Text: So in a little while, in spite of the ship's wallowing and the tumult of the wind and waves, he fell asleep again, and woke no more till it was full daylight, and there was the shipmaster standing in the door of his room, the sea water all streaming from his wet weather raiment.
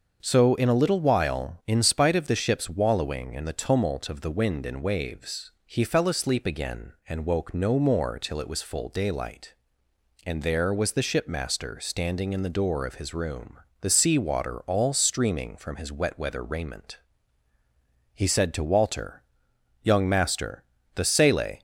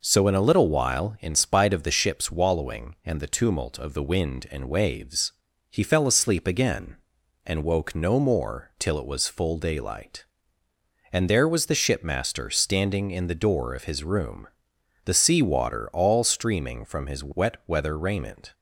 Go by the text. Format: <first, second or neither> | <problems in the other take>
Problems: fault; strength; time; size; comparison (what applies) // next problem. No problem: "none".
second | starts louder than the rest; until 1.2 s; 6.5 dB // goes on to say "He said to Walter Young master the sele"; strong; from 18.1 s on; 3.4 s long